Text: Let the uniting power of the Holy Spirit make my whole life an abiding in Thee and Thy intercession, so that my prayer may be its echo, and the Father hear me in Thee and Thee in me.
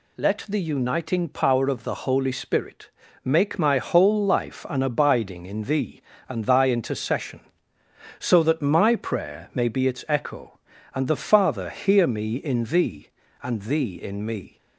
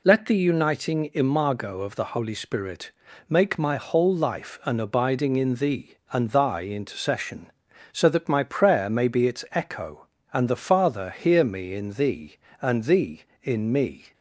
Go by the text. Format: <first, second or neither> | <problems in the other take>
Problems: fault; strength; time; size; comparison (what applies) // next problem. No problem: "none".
first | says "imago" for "power"; at 1.1 s // pauses between "Spirit" and "make"; slight; at 2.9 s; 0.36 s long; slight in the first